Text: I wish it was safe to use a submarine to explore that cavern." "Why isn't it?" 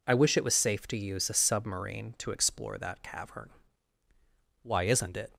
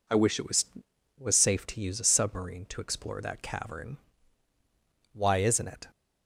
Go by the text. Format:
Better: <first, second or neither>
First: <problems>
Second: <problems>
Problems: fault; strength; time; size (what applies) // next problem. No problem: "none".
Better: first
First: none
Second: says "was" twice; at 1.1 s